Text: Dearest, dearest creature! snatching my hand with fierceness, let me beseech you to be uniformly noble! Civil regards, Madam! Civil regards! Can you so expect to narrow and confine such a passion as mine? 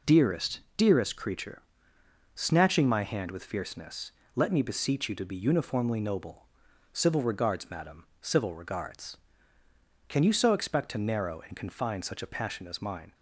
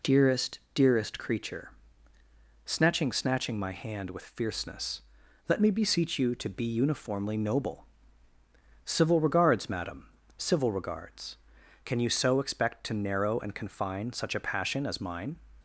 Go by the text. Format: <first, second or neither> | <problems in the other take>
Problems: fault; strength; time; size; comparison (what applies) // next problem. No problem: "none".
first | says "snatching" twice; at 3.1 s